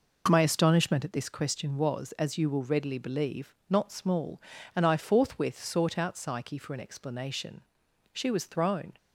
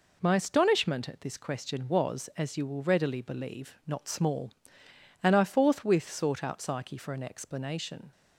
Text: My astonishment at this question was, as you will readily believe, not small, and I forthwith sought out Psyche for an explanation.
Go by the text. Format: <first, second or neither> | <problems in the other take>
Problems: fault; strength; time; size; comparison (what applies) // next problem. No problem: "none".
second | goes on to say "She was thrown"; noticeable; from 8.1 s on; 0.80 s long